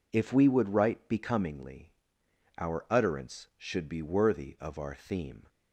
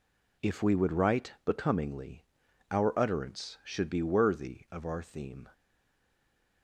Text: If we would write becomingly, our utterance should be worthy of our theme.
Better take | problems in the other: first | stays silent after the last word; from 5.5 s on; 1.1 s long

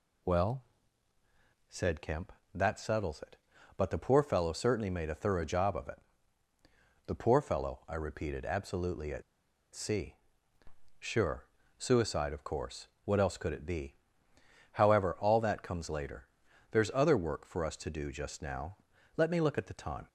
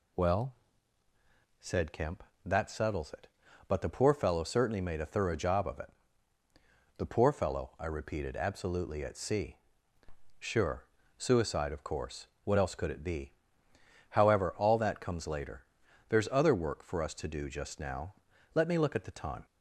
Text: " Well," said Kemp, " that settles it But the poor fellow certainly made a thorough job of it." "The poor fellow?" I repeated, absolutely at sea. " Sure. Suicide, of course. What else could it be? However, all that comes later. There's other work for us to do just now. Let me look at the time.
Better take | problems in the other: second | pauses between "at" and "sea"; noticeable; at 9.2 s; 0.52 s long

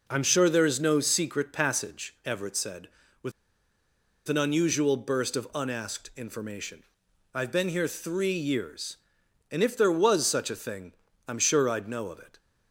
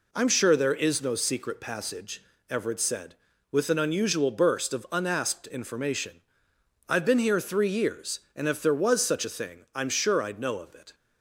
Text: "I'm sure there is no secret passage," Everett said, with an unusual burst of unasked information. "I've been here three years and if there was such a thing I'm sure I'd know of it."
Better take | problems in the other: second | pauses between "with" and "an"; noticeable; at 3.3 s; 0.96 s long // pauses between "thing" and "I'm"; slight; at 10.9 s; 0.34 s long

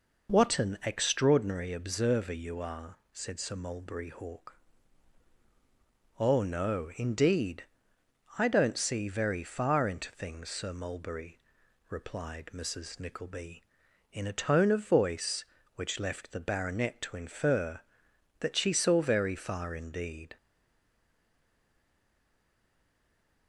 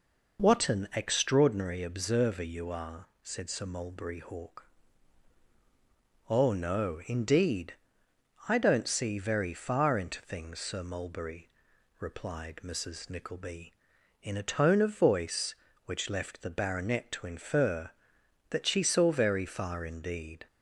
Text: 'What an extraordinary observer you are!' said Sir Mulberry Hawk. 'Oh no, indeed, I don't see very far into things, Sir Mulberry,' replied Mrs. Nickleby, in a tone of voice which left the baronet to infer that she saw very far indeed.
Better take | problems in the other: second | stays silent after the last word; strong; from 20.3 s on; 3.1 s long

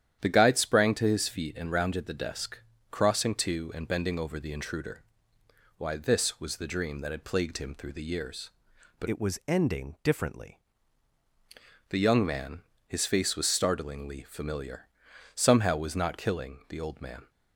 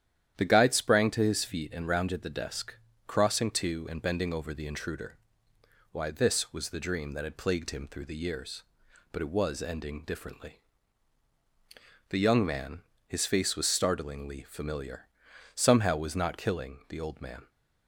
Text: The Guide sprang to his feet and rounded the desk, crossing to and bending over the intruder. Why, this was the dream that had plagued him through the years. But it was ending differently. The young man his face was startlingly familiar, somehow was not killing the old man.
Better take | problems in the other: second | starts louder than the rest; strong; until 1.2 s; 10 dB; strong in the second // changes voice from "it" to "differently"; from 9.0 to 10.5 s; 1.5 s long // pauses between "man" and "his"; slight; at 12.6 s; 0.26 s long; slight in the second

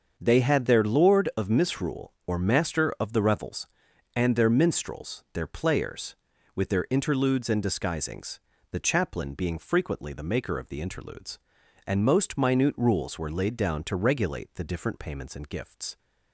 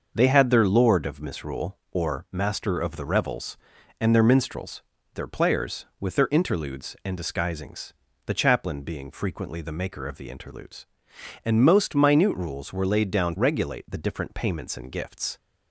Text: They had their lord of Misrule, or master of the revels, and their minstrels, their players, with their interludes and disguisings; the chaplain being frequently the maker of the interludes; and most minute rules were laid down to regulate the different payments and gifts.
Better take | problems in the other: first | starts louder than the rest; noticeable; until 1.1 s; 6 dB; also in the first // skips "to"; at 13.3 s

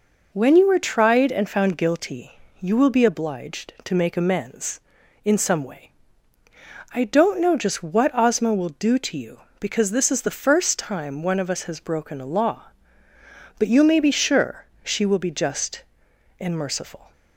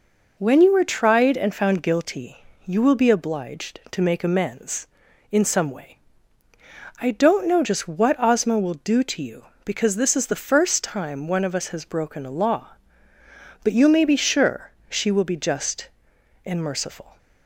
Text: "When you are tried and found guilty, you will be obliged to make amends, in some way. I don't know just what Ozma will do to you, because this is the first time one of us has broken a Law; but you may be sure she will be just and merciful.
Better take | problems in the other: neither | pauses between "sure" and "she"; slight; the same in both

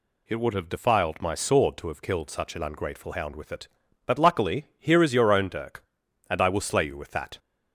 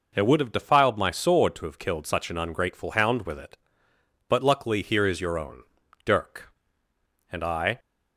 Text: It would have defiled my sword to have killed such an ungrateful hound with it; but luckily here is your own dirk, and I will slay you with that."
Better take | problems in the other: first | pauses between "own" and "dirk"; at 5.6 s; 0.42 s long // stops before "will slay you with that"; at 7.7 s

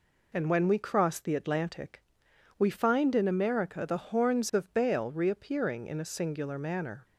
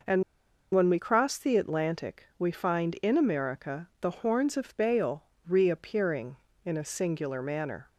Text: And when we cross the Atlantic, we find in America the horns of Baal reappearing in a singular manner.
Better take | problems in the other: first | pauses between "And" and "when"; noticeable; at 0.2 s; 0.51 s long // pauses between "Baal" and "reappearing"; slight; at 5.2 s; 0.24 s long

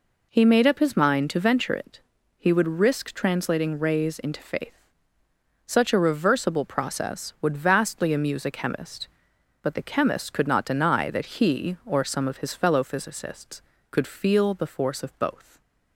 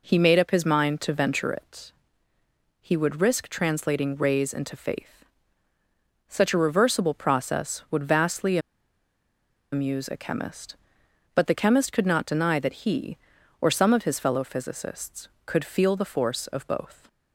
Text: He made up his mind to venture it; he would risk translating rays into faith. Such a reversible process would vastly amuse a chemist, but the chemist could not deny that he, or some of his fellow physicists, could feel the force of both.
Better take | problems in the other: first | pauses between "vastly" and "amuse"; at 8.5 s; 1.1 s long

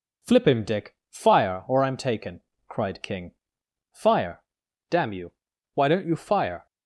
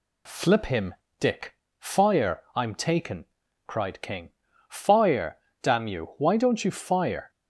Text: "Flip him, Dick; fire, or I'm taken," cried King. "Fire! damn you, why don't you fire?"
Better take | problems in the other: first | skips "or"; at 2.4 s

